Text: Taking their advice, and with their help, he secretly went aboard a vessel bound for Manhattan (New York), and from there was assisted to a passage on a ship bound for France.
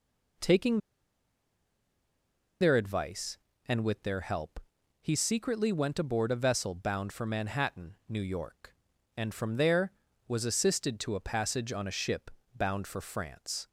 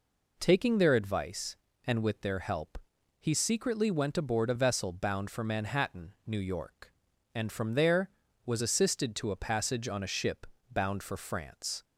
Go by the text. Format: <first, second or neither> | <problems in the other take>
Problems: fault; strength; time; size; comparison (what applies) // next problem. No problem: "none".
second | pauses between "Taking" and "their"; strong; at 0.7 s; 1.8 s long // pauses between "ship" and "bound"; slight; at 12.3 s; 0.26 s long; slight in the second